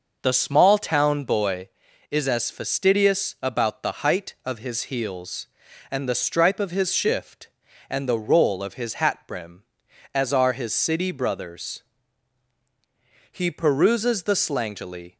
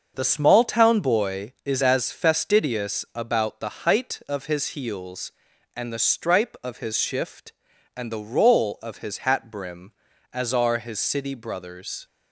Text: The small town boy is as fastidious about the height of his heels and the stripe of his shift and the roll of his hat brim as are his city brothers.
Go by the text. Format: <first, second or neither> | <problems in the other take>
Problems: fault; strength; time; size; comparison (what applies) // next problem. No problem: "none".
second | starts louder than the rest; noticeable; until 1.2 s; 6 dB; also in the second // goes on to say "He peruses the slangily"; strong; from 13.3 s on; 1.8 s long